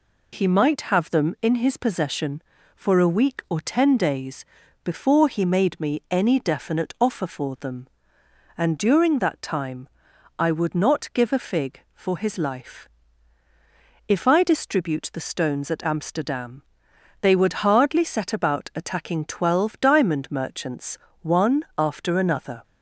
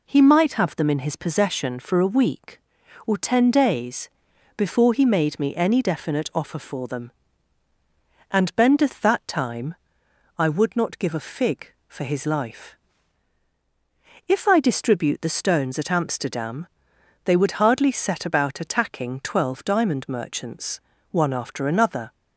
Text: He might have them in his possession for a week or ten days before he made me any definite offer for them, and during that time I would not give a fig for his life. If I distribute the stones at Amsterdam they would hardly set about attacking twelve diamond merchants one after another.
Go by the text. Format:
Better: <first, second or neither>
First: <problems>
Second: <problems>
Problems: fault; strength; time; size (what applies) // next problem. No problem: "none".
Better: first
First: pauses between "days" and "before"; at 4.4 s; 0.40 s long // pauses between "time" and "I"; noticeable; at 9.8 s; 0.50 s long // pauses between "Amsterdam" and "they"; noticeable; at 16.6 s; 0.62 s long // pauses between "merchants" and "one"; slight; at 20.9 s; 0.24 s long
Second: pauses between "days" and "before"; noticeable; at 4.0 s; 0.46 s long // says "bendeth" for "during"; at 8.5 s // pauses between "time" and "I"; noticeable; at 9.7 s; 0.62 s long // pauses between "Amsterdam" and "they"; noticeable; at 16.6 s; 0.58 s long // pauses between "merchants" and "one"; slight; at 20.8 s; 0.30 s long